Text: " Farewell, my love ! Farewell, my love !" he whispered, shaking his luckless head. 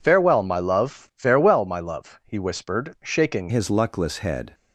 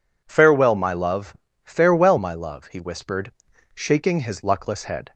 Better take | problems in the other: second | changes voice at "his"; from 3.4 s on; 1.1 s long

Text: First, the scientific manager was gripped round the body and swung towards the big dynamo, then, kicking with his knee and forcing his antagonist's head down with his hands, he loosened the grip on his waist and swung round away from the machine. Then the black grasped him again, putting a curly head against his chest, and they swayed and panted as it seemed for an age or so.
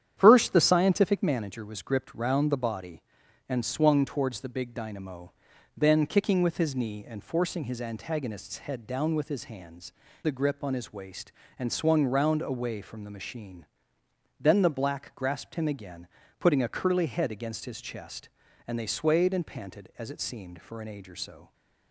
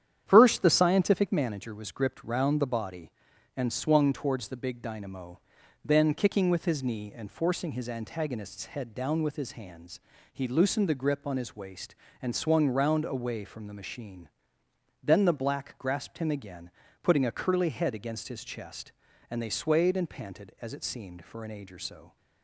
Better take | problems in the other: second | starts louder than the rest; strong; until 1.1 s; 9.5 dB; strong in the second // skips "he loosened"; at 10.0 s

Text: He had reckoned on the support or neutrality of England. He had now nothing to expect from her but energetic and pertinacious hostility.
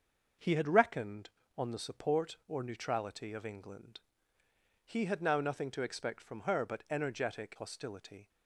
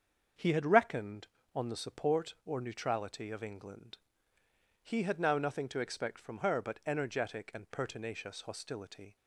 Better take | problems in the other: second | starts louder than the rest; until 1.7 s; 6.5 dB; also in the second // skips "and pertinacious"; at 7.5 s

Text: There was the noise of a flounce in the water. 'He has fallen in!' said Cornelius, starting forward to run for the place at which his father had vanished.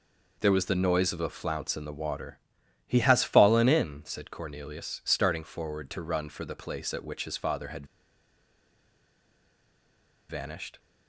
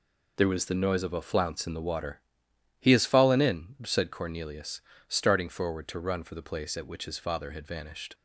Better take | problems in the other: second | pauses between "had" and "vanished"; strong; at 7.8 s; 2.4 s long

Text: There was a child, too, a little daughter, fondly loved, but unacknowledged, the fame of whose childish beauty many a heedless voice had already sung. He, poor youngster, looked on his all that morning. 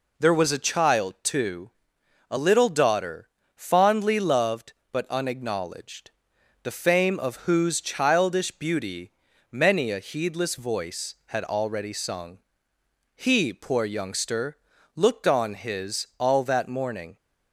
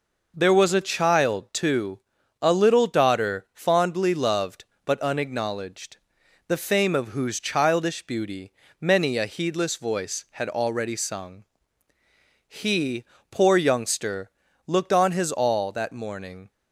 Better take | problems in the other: neither | pauses between "beauty" and "many"; the same in both

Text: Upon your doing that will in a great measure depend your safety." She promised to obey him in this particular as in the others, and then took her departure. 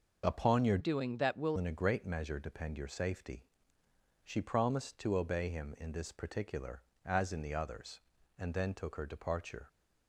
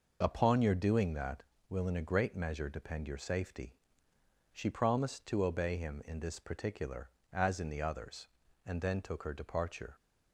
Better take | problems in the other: second | changes voice from "doing" to "will"; from 0.7 to 1.5 s; 0.8 s long

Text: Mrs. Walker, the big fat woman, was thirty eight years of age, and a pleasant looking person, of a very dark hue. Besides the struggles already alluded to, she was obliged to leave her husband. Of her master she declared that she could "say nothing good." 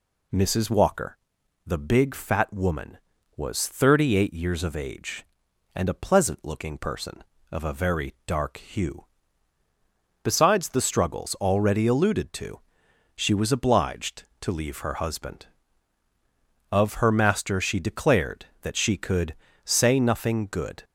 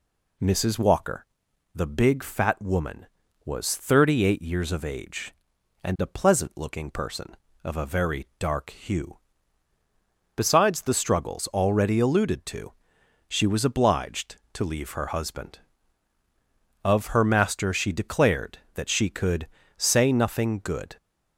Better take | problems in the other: neither | pauses between "could" and "say"; slight; the same in both

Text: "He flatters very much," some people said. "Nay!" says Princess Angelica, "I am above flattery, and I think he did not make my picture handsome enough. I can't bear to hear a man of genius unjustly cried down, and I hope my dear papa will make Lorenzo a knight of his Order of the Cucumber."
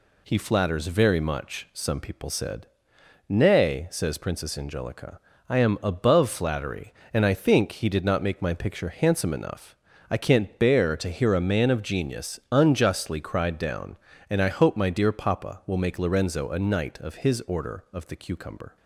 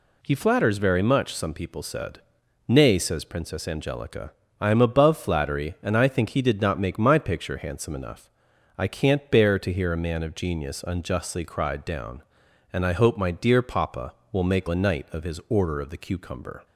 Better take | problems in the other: first | skips "Lorenzo"; at 14.6 s

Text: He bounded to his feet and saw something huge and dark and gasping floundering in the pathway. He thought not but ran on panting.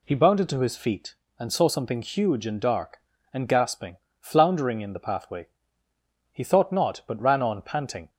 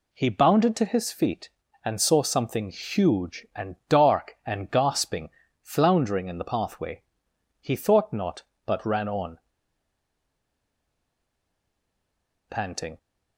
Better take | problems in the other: first | pauses between "gasping" and "floundering"; slight; at 5.3 s; 0.32 s long; slight in the first // pauses between "on" and "panting"; strong; at 9.3 s; 3.1 s long

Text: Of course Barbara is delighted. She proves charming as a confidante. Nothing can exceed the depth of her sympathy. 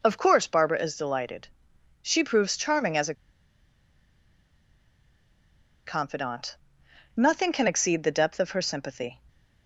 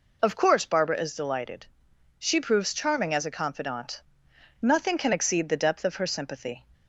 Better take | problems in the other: second | pauses between "a" and "confidante"; strong; at 3.1 s; 2.7 s long

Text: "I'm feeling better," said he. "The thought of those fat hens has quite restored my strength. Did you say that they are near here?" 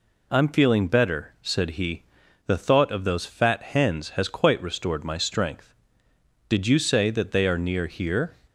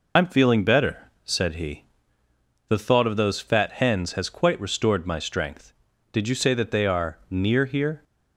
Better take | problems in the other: first | loses the start of "I'm"; at 0.1 s; 110 ms

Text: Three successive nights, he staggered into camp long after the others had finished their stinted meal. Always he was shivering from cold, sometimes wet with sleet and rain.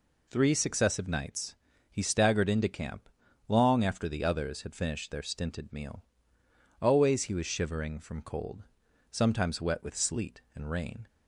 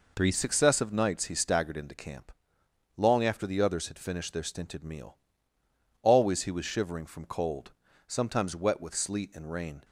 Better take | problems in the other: first | changes voice at "successive"; from 0.3 s on; 9.5 s long // pauses between "camp" and "long"; noticeable; at 2.3 s; 0.66 s long; also in the first

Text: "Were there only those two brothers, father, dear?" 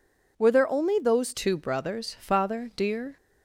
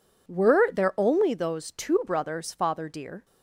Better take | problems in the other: second | changes voice at "two"; from 1.3 s on; 1.8 s long

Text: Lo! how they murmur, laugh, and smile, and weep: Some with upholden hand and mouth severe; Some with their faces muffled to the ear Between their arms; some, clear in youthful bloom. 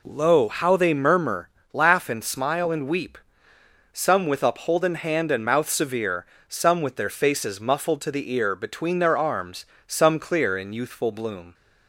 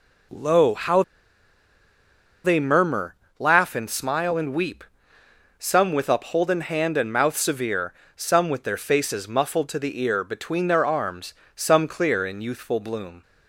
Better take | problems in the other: first | pauses between "how" and "they"; strong; at 1.0 s; 1.4 s long

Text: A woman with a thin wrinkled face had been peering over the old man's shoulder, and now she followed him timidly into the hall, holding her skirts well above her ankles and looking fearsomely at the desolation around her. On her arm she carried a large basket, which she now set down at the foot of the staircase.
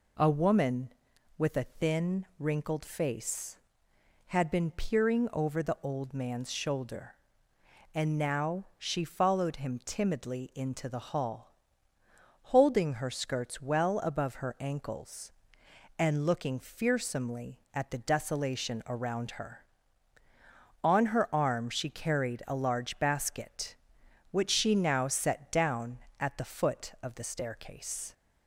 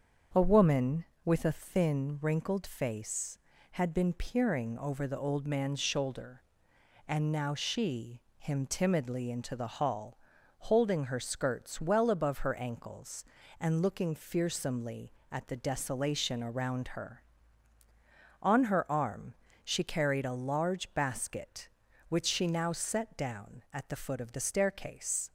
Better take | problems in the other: first | starts louder than the rest; until 1.5 s; 7 dB // skips "followed"; at 8.3 s // pauses between "arm" and "she"; slight; at 19.3 s; 0.30 s long

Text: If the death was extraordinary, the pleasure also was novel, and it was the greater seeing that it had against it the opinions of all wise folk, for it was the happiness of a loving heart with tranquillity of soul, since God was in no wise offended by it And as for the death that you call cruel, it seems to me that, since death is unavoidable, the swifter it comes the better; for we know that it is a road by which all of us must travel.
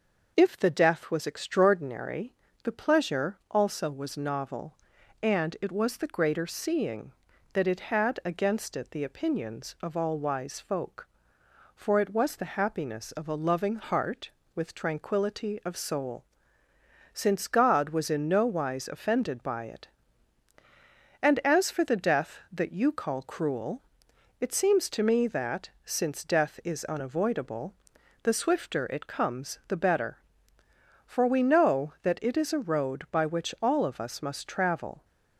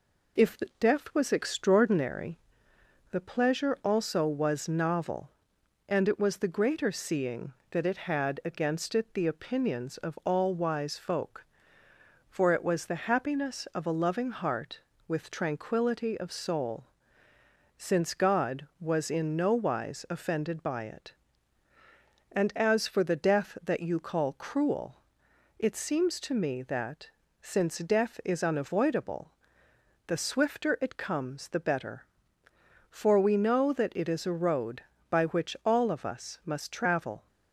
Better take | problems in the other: neither | none

